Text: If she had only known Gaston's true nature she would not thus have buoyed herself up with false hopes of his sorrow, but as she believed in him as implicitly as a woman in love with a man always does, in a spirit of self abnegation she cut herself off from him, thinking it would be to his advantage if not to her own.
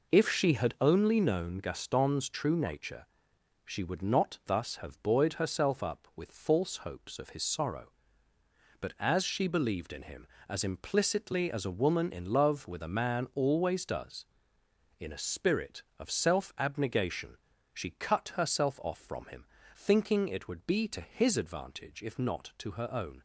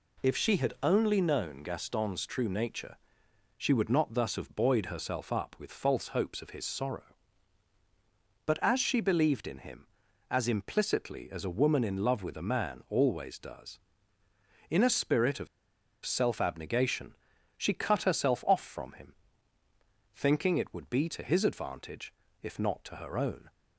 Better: first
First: pauses between "nature" and "she"; noticeable; at 3.0 s; 0.60 s long // pauses between "abnegation" and "she"; slight; at 17.3 s; 0.34 s long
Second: pauses between "nature" and "she"; noticeable; at 2.9 s; 0.60 s long // pauses between "of" and "self"; noticeable; at 15.4 s; 0.58 s long // pauses between "abnegation" and "she"; at 17.1 s; 0.42 s long // pauses between "advantage" and "if"; slight; at 22.1 s; 0.30 s long

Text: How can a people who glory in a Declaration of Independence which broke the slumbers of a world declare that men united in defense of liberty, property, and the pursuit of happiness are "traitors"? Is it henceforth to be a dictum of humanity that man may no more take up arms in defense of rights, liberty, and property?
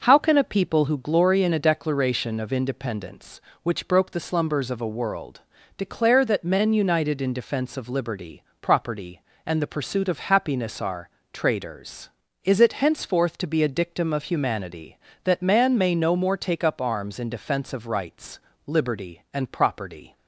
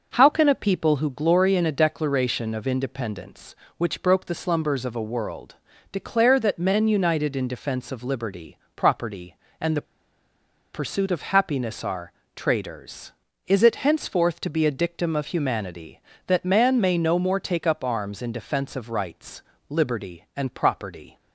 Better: first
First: pauses between "world" and "declare"; slight; at 5.3 s; 0.36 s long // pauses between "are" and "traitors"; slight; at 11.0 s; 0.24 s long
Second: pauses between "world" and "declare"; slight; at 5.5 s; 0.36 s long // pauses between "the" and "pursuit"; noticeable; at 9.8 s; 0.91 s long // pauses between "are" and "traitors"; slight; at 12.1 s; 0.24 s long

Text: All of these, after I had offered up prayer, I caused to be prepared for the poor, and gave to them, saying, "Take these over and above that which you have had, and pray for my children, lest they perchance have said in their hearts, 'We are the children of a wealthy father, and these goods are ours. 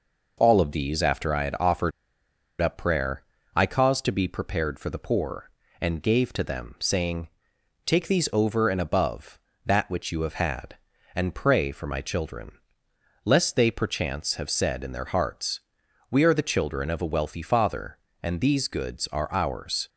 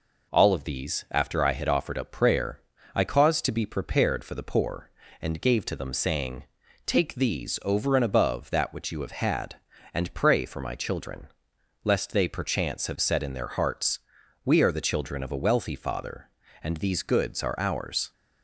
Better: second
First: pauses between "offered" and "up"; noticeable; at 1.9 s; 0.69 s long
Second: none

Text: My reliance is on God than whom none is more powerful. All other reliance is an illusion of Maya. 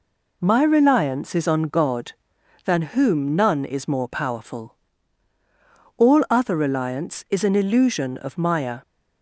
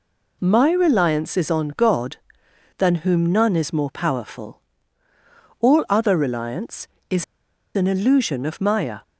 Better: first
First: none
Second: pauses between "is" and "an"; noticeable; at 7.2 s; 0.50 s long

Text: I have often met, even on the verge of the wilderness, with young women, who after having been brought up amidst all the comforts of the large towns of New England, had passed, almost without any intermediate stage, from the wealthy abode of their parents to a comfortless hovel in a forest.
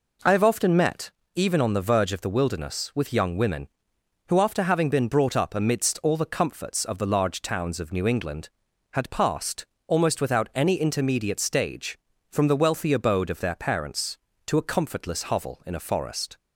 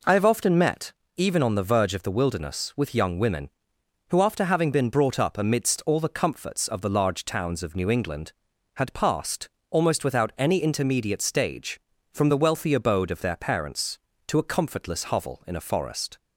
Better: neither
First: none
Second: none

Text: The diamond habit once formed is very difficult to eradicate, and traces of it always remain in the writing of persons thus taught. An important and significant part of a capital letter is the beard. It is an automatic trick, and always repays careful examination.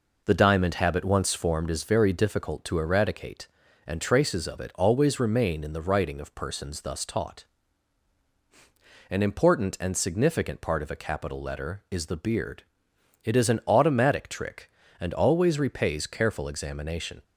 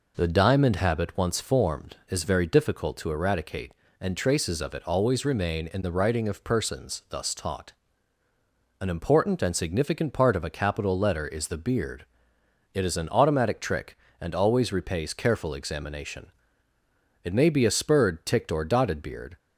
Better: first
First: none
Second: goes on to say "It may be a spurred ticked or dotted beard"; strong; from 17.2 s on; 2.1 s long

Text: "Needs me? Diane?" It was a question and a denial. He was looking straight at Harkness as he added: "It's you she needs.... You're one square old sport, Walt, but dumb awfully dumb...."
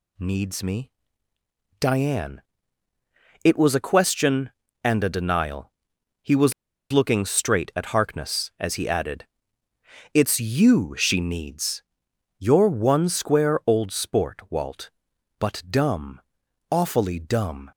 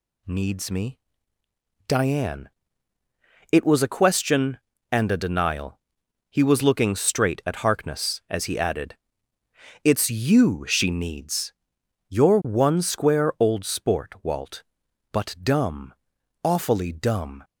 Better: second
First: pauses between "was" and "looking"; at 6.5 s; 0.40 s long // pauses between "dumb" and "awfully"; noticeable; at 16.2 s; 0.48 s long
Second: pauses between "dumb" and "awfully"; noticeable; at 15.9 s; 0.48 s long

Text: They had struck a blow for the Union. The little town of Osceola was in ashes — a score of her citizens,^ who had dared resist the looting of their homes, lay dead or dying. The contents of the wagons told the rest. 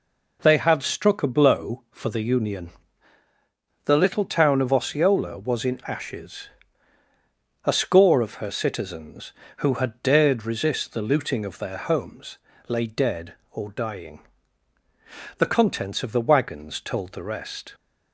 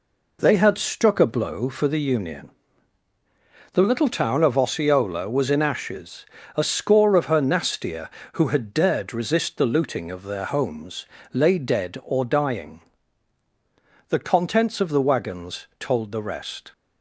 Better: first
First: none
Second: says "nastier" for "citizens"; at 7.4 s

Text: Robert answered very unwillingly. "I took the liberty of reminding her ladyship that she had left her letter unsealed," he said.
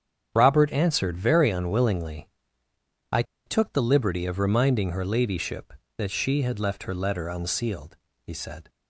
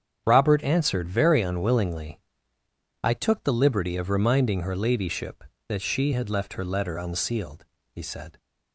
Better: second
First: starts louder than the rest; strong; until 1.3 s; 8 dB // pauses between "I" and "took"; slight; at 3.2 s; 0.23 s long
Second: starts louder than the rest; strong; until 1.2 s; 8 dB

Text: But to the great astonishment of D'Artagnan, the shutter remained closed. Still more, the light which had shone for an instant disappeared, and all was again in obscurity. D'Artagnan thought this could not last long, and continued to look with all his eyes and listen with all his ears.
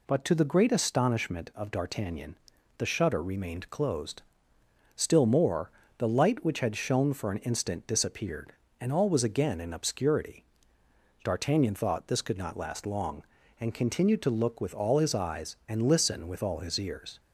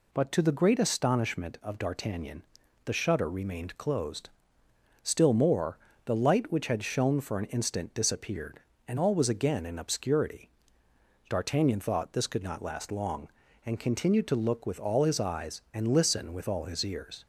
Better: neither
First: none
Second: none

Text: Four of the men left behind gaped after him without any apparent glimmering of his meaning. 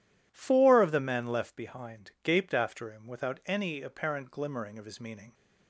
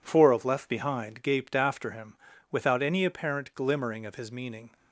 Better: first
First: none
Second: skips "the men"; at 0.4 s // pauses between "him" and "without"; slight; at 2.1 s; 0.36 s long

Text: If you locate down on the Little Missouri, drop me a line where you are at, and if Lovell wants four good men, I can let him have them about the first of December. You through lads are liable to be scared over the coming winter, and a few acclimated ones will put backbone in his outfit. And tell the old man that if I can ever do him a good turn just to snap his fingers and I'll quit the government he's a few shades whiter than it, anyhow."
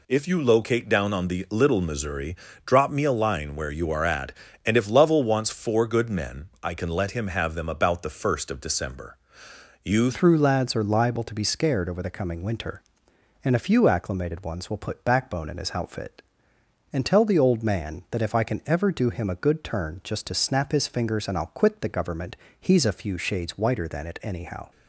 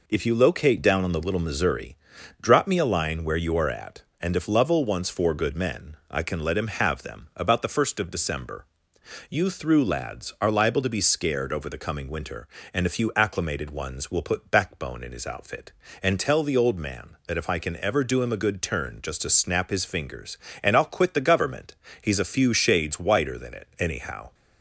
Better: second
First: changes voice at "through"; from 10.1 s on; 14.6 s long // pauses between "government" and "he's"; slight; at 22.3 s; 0.24 s long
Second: pauses between "government" and "he's"; slight; at 21.7 s; 0.26 s long

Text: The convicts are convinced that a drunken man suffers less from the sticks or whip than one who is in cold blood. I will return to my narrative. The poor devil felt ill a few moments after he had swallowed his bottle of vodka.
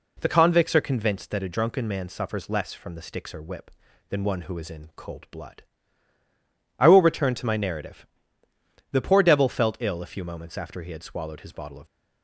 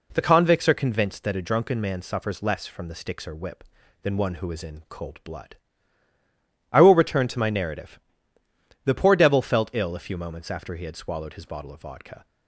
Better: second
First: stops before "vodka"; at 11.8 s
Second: none

